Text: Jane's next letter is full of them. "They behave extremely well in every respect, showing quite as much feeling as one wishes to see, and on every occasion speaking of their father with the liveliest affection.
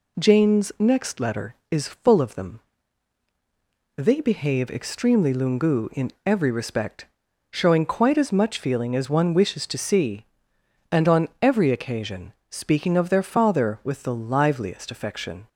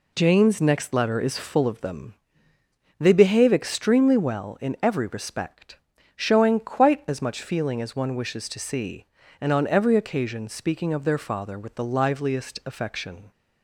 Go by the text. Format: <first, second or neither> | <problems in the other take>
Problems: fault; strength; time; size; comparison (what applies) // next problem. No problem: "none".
second | says "lungu" for "well"; at 5.3 s // pauses between "occasion" and "speaking"; slight; at 12.3 s; 0.16 s long